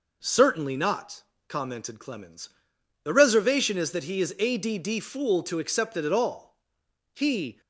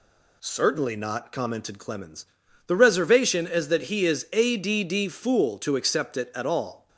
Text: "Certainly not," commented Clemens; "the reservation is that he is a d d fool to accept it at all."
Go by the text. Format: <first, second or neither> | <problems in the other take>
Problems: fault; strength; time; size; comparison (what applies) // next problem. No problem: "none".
second | goes on to say "He"; slight; from 7.1 s on; 0.46 s long